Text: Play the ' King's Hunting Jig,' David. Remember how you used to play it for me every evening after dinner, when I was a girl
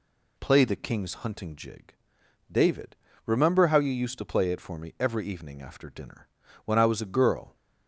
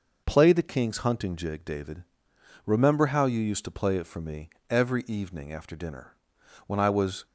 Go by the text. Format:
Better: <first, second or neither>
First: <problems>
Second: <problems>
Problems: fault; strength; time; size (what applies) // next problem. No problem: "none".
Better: first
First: none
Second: pauses between "me" and "every"; slight; at 4.4 s; 0.22 s long // stops before "a girl"; at 7.2 s